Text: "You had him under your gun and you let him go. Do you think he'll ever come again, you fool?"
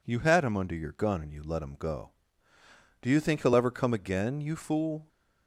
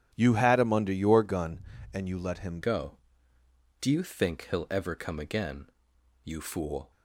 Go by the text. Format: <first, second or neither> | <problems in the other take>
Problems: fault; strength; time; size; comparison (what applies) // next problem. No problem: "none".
first | starts louder than the rest; strong; until 1.1 s; 10.5 dB // changes voice at "go"; from 2.6 s on; 4.3 s long